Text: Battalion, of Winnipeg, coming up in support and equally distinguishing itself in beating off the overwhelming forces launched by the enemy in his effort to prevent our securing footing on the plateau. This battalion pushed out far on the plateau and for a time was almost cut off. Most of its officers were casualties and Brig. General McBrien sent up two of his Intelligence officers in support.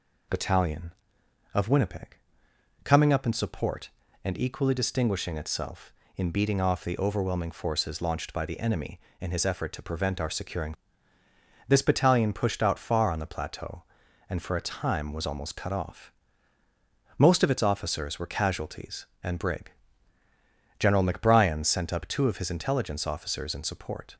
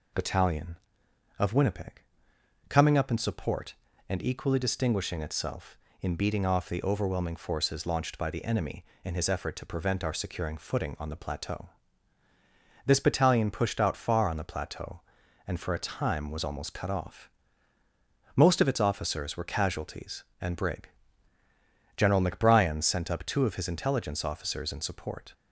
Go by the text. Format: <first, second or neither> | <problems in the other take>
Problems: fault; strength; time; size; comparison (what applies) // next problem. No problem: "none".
second | skips "footing on the plateau"; at 11.2 s